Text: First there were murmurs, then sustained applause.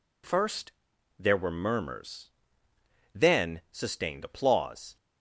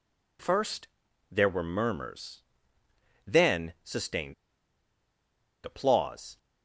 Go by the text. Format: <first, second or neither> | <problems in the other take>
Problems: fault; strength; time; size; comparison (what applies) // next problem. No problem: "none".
first | pauses between "First" and "there"; at 0.8 s; 0.44 s long; noticeable in the first // pauses between "sustained" and "applause"; strong; at 4.3 s; 1.3 s long